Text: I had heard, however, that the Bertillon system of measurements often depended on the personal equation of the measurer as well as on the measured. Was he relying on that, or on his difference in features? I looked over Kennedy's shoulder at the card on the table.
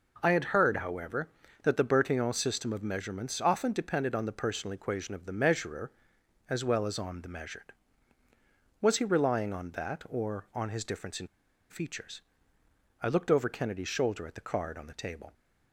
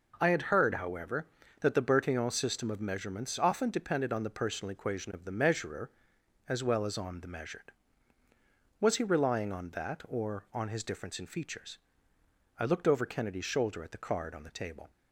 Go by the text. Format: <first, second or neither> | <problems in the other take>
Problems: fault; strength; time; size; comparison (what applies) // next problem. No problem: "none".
second | pauses between "in" and "features"; at 11.2 s; 0.43 s long